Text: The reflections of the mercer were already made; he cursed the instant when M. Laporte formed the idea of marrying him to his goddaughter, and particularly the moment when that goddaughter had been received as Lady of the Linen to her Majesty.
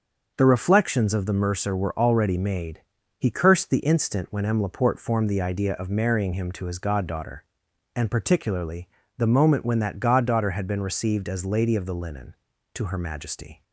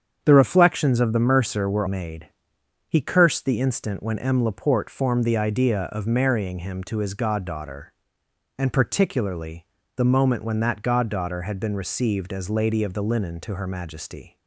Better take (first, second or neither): first